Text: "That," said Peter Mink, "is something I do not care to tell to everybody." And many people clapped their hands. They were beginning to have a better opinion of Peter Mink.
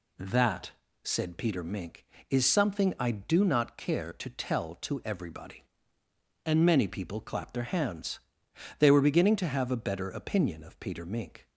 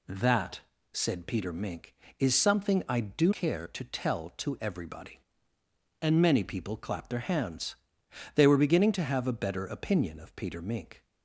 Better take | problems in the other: first | skips "not"; at 3.3 s

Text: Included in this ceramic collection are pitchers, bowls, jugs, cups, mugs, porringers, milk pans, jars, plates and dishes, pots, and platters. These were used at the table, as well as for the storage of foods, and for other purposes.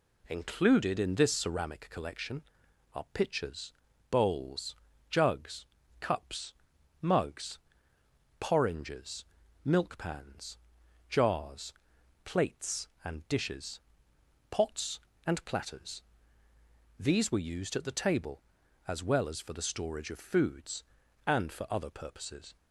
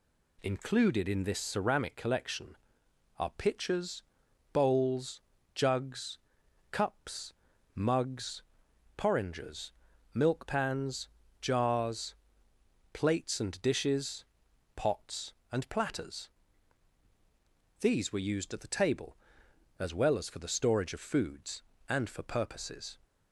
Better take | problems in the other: first | skips "other"; at 22.2 s

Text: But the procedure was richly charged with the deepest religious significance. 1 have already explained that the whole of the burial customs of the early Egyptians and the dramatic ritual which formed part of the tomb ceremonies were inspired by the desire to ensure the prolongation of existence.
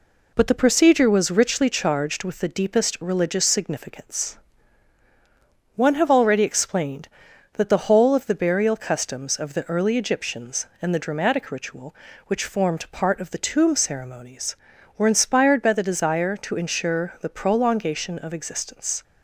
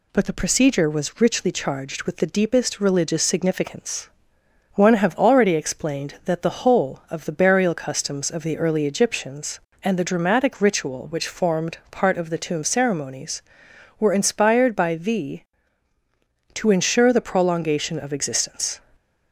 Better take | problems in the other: first | skips "desire"; at 15.9 s

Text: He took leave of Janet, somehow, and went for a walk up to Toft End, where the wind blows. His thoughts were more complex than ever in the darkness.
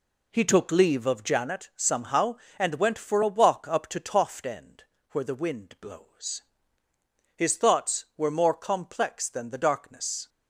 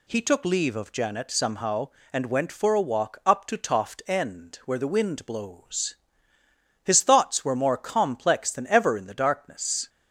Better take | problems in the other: second | skips "ever in"; at 9.4 s

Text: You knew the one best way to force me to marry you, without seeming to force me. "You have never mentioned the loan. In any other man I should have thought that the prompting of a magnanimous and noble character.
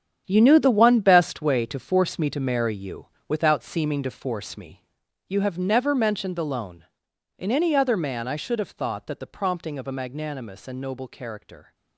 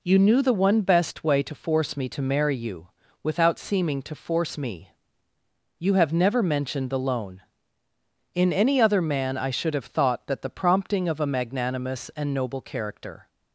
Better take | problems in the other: second | gets quieter; strong; throughout; 12.5 dB

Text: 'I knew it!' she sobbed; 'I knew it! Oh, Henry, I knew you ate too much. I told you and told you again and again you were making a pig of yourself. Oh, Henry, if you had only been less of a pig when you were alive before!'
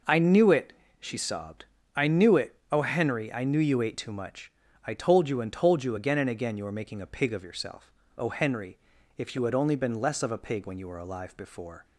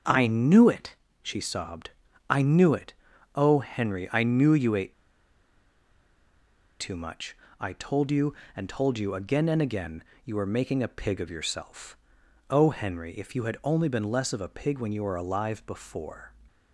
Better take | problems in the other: first | starts louder than the rest; until 1.3 s; 6.5 dB // pauses between "ate" and "too"; strong; at 4.9 s; 1.8 s long // pauses between "again" and "you"; slight; at 10.0 s; 0.22 s long

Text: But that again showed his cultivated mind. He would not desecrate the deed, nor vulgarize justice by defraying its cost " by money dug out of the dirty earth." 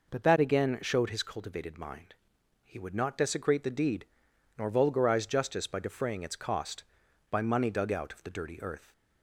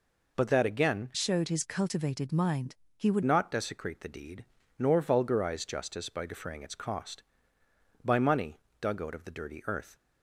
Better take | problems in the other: first | changes voice from "showed" to "would"; from 1.1 to 3.2 s; 2.1 s long // pauses between "money" and "dug"; slight; at 8.5 s; 0.22 s long

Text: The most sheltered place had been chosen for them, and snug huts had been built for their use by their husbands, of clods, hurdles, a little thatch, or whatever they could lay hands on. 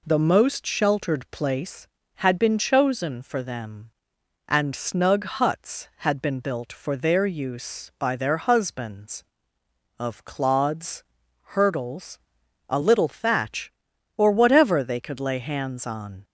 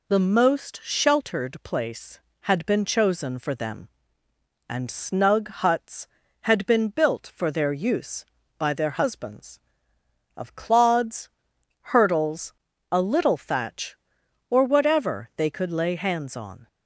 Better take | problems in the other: neither | none

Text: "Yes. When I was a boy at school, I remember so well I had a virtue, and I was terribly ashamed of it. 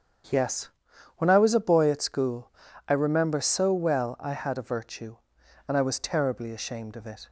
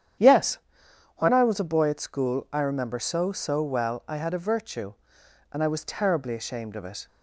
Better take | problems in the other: first | starts louder than the rest; strong; until 1.8 s; 9.5 dB; strong in the first // says "so" twice; at 3.2 s

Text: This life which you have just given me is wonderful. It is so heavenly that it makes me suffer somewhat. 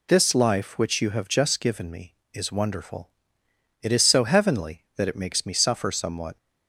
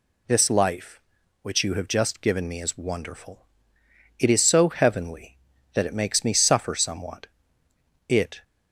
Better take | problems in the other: first | goes on to say "It"; slight; from 8.0 s on; 0.36 s long

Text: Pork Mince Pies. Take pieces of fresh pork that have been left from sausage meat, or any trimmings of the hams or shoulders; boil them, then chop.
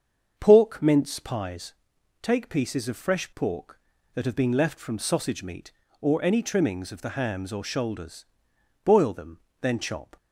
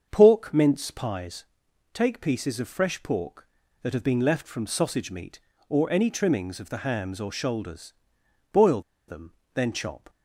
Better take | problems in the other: first | starts louder than the rest; until 1.1 s; 7 dB; also in the first // pauses between "boil" and "them"; slight; at 8.8 s; 0.27 s long

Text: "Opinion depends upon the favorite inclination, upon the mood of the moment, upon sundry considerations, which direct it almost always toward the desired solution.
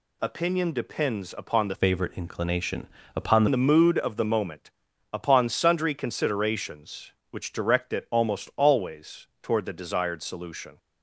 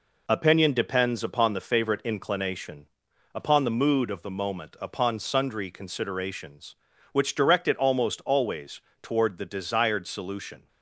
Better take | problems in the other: second | changes voice from "favorite" to "upon"; from 1.7 to 3.4 s; 1.7 s long // pauses between "always" and "toward"; slight; at 9.2 s; 0.16 s long; slight in the second

